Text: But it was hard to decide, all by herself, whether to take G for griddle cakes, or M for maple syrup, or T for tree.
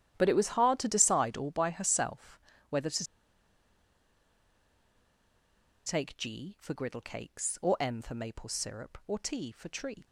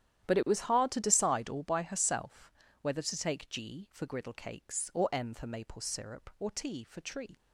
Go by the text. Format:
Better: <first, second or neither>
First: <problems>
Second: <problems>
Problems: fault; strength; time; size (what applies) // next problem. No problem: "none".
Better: second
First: starts louder than the rest; strong; until 1.1 s; 11 dB // pauses between "to" and "take"; strong; at 3.0 s; 2.8 s long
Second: starts louder than the rest; strong; until 1.3 s; 11 dB